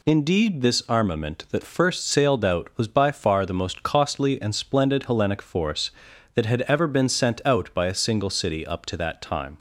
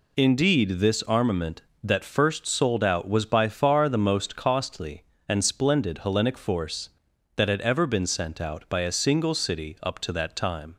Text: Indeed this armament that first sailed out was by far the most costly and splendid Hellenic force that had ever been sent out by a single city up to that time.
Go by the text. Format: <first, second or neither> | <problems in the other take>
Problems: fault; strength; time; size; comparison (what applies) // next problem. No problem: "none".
first | says "sold" for "sailed"; at 2.4 s